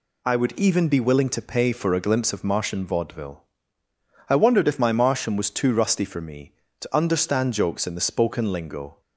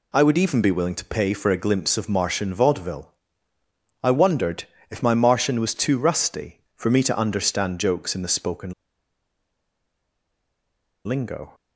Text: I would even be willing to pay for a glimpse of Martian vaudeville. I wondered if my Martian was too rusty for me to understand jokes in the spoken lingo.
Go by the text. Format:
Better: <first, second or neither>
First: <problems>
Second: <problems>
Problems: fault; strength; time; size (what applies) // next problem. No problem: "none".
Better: first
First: none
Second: pauses between "wondered" and "if"; slight; at 4.6 s; 0.26 s long // pauses between "spoken" and "lingo"; strong; at 8.7 s; 2.3 s long